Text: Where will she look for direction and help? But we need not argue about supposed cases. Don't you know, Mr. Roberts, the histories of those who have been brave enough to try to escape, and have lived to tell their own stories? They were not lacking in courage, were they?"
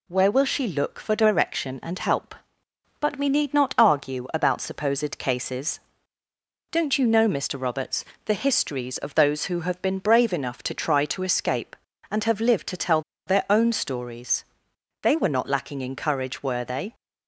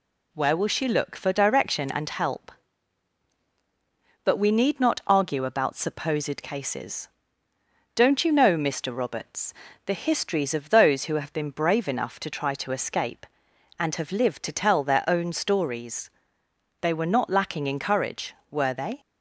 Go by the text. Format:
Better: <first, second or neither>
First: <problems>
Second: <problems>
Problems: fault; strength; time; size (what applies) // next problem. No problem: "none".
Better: second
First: pauses between "tell" and "their"; slight; at 13.0 s; 0.26 s long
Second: none